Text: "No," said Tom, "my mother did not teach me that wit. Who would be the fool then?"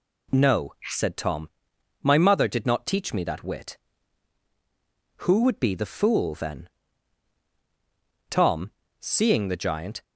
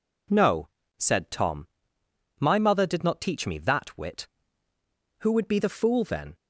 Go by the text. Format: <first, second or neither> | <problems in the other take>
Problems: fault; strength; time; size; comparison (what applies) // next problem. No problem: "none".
second | goes on to say "Tom seeing the giant"; strong; from 8.2 s on; 1.7 s long